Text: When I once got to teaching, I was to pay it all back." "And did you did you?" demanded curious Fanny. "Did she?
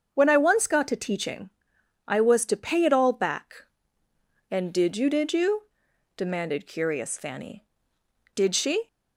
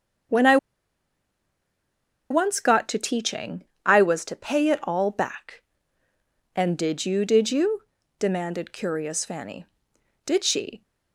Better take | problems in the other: first | starts louder than the rest; strong; until 3.0 s; 7.5 dB; also in the first // pauses between "I" and "once"; strong; at 0.5 s; 1.7 s long

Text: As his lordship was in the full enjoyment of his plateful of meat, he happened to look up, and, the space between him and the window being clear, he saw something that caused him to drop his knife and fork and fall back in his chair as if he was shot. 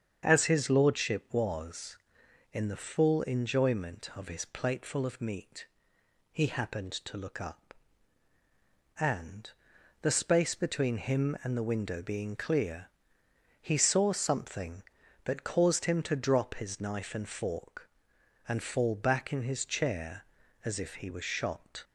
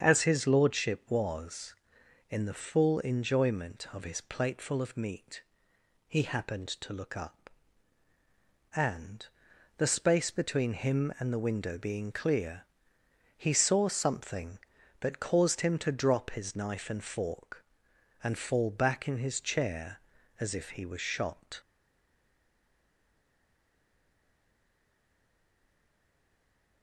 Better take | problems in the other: first | starts louder than the rest; strong; until 1.0 s; 7.5 dB; strong in the first // stays silent after the last word; strong; from 21.6 s on; 5.2 s long

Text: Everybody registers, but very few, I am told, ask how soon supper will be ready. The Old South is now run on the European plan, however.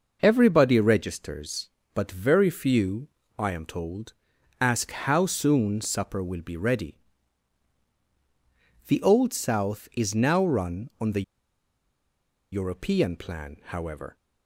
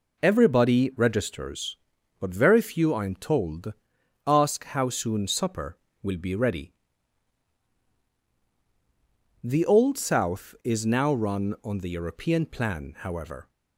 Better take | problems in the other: second | pauses between "the" and "European"; strong; at 11.2 s; 1.3 s long

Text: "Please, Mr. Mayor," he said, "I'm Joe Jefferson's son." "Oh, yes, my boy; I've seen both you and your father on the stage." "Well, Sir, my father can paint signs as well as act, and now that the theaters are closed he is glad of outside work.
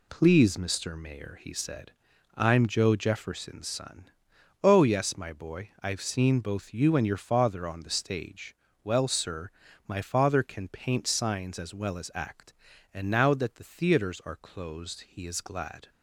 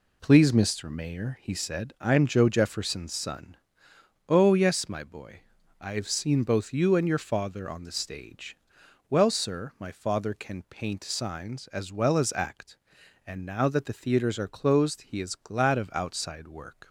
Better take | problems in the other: second | stops before "of outside work"; at 15.8 s

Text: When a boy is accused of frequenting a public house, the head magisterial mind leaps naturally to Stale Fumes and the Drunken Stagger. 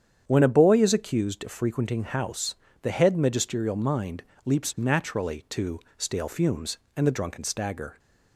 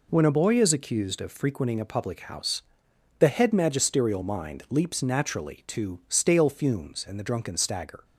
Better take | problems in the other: second | starts louder than the rest; strong; until 1.2 s; 8.5 dB // skips "a public"; at 2.0 s // pauses between "mind" and "leaps"; slight; at 4.2 s; 0.20 s long // pauses between "to" and "Stale"; slight; at 5.7 s; 0.18 s long

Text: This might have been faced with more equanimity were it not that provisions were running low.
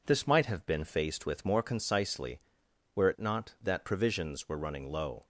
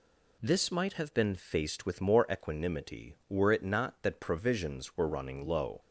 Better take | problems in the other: second | says "concisely" for "equanimity"; at 1.6 s

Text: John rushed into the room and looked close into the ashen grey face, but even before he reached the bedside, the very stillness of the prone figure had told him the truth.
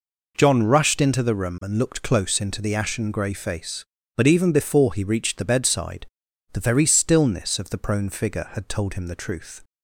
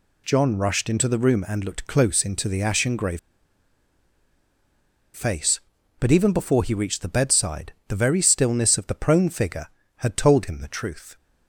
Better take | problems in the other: first | pauses between "grey" and "face"; strong; at 3.1 s; 1.9 s long

